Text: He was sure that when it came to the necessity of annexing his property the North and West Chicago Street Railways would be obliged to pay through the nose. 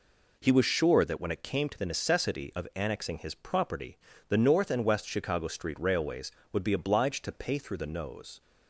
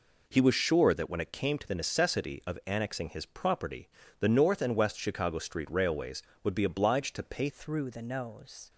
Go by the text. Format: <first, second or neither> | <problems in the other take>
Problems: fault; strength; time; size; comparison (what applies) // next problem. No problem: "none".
first | pauses between "property" and "the"; slight; at 3.8 s; 0.30 s long; slight in the first // changes voice at "through"; from 7.4 s on; 1.2 s long